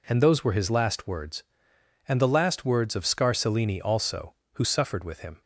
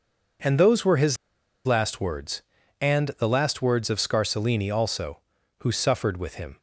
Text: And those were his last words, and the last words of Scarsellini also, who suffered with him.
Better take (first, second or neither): first